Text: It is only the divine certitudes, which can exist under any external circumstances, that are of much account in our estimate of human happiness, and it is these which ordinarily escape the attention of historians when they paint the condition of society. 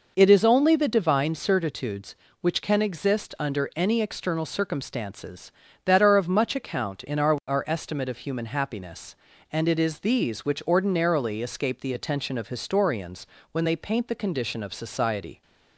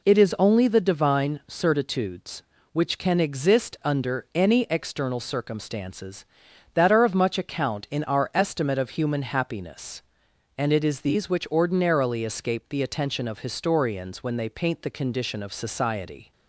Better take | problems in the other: second | says "our" twice; at 7.4 s // pauses between "historians" and "when"; slight; at 13.2 s; 0.28 s long

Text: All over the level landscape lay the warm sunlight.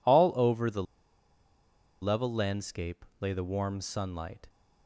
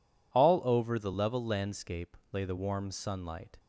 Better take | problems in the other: second | pauses between "the" and "level"; at 0.8 s; 1.1 s long // pauses between "landscape" and "lay"; slight; at 3.0 s; 0.16 s long; slight in the second

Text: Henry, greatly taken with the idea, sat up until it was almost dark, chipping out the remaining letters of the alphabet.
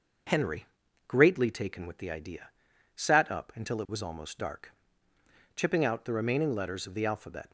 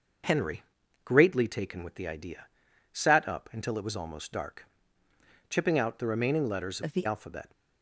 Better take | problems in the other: first | changes voice from "of" to "the"; from 6.8 to 7.0 s; 0.2 s long

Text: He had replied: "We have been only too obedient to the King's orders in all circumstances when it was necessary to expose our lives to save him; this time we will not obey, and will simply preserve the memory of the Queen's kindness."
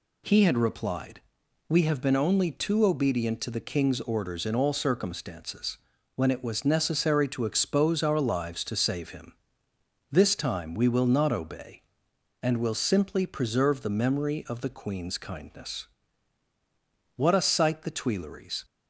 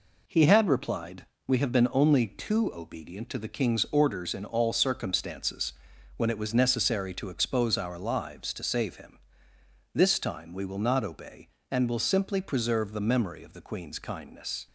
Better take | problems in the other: second | pauses between "circumstances" and "when"; at 5.7 s; 0.38 s long; also in the second // goes on to say "What a sight the Tuileries"; from 17.1 s on; 1.4 s long

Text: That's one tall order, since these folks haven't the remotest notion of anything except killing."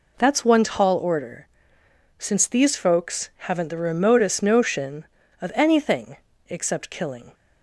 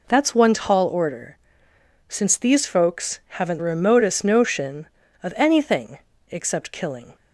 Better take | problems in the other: first | skips "the"; at 3.5 s // pauses between "anything" and "except"; slight; at 5.9 s; 0.30 s long; slight in the first

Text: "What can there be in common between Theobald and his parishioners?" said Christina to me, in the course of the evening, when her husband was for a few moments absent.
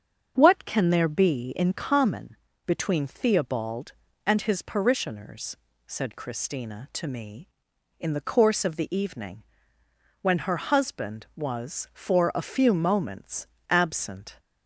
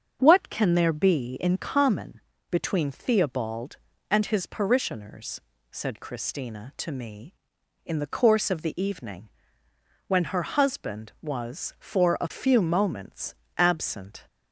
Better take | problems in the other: neither | starts louder than the rest; strong; the same in both // pauses between "common" and "between"; slight; the same in both // pauses between "moments" and "absent"; slight; the same in both

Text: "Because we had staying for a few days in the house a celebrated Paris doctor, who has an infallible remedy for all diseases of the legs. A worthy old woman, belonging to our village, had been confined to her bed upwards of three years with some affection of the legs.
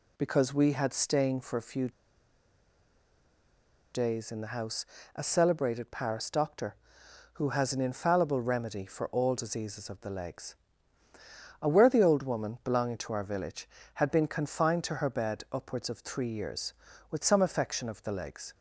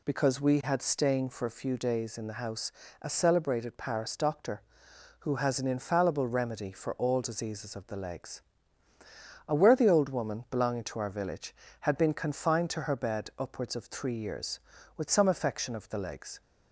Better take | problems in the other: second | pauses between "few" and "days"; strong; at 1.8 s; 2.0 s long // pauses between "house" and "a"; slight; at 4.8 s; 0.30 s long; slight in the second

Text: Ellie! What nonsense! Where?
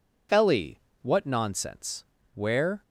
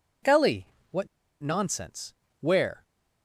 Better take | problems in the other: first | pauses between "What" and "nonsense"; slight; at 1.0 s; 0.33 s long

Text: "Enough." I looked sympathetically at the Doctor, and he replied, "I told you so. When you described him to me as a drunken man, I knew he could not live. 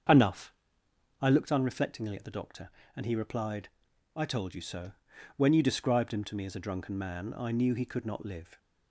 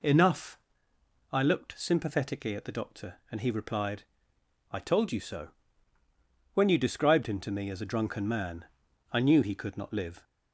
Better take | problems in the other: second | starts louder than the rest; until 1.7 s; 6.5 dB // says "unreflectingly" for "sympathetically"; at 1.5 s

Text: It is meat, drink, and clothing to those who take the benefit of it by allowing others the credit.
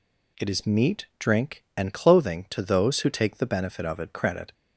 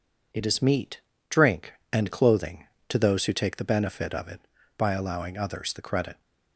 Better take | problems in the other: second | skips "by allowing others the"; at 4.1 s

